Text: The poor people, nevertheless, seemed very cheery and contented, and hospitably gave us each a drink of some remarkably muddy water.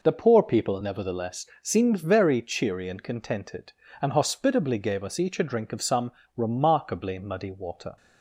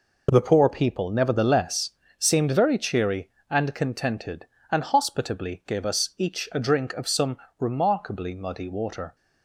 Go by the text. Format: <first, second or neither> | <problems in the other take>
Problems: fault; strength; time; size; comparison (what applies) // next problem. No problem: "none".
neither | pauses between "some" and "remarkably"; slight; the same in both